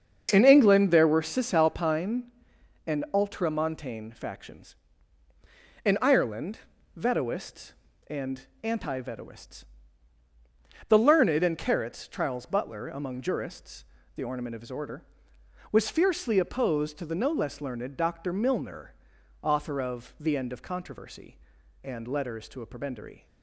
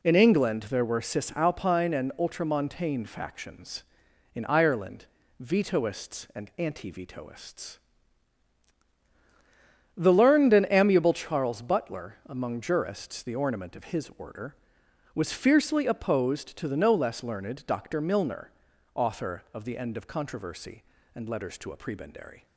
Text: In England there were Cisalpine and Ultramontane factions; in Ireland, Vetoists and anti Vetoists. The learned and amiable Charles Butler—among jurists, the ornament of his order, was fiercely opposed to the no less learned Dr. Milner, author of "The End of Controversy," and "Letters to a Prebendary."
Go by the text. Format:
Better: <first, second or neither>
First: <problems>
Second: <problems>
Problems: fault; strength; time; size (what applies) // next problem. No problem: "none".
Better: second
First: starts louder than the rest; until 1.3 s; 7 dB // pauses between "and" and "anti"; slight; at 8.4 s; 0.16 s long // says "carrots" for "amiable"; at 11.5 s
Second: none